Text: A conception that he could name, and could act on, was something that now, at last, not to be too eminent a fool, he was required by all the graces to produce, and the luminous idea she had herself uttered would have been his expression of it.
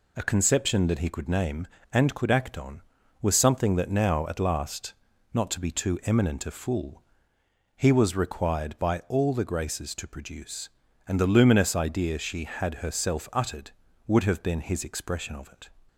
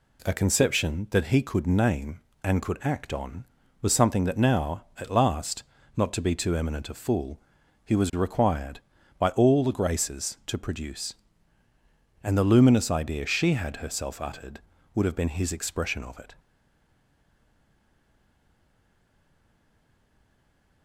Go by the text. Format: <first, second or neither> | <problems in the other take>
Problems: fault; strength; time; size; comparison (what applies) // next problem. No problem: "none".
first | stays silent after the last word; strong; from 16.3 s on; 4.5 s long